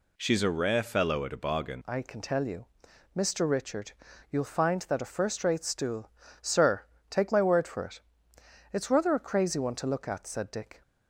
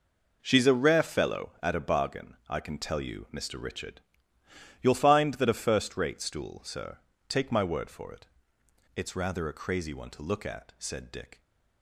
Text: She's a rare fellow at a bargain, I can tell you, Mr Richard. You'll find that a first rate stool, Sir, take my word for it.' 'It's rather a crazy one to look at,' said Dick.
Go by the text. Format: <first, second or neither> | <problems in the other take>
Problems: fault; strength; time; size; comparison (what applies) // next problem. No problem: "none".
second | changes voice at "I"; from 1.8 s on; 9.0 s long